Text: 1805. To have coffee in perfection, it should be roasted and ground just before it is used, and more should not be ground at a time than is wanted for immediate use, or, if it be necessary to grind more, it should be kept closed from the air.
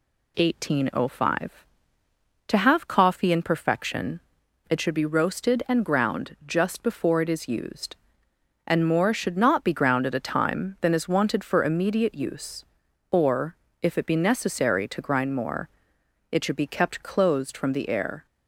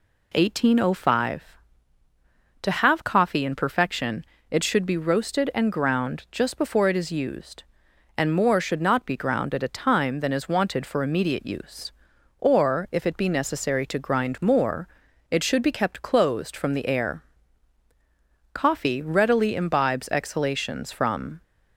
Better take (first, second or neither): first